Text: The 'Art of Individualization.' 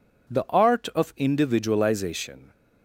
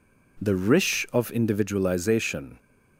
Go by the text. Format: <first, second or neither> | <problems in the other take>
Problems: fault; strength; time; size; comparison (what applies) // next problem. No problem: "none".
first | says "Rish" for "Art"; at 0.5 s